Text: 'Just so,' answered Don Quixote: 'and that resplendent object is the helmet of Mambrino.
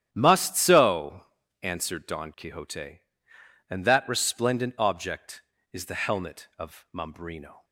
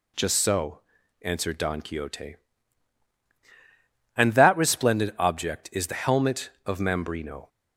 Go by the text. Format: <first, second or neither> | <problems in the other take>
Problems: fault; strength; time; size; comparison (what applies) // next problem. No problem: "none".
second | starts louder than the rest; strong; until 1.1 s; 10.5 dB // says "Must" for "Just"; at 0.1 s